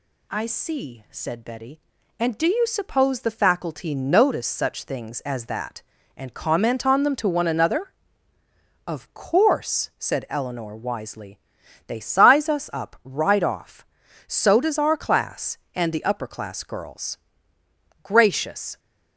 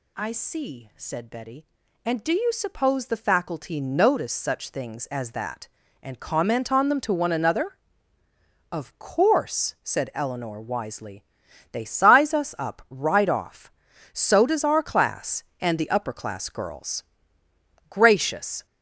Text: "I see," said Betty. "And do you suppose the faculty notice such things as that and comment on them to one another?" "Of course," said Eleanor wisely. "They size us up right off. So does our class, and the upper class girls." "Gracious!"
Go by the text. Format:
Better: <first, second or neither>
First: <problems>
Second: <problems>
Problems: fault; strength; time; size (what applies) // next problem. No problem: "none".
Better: first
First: none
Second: gets louder; noticeable; throughout; 4.5 dB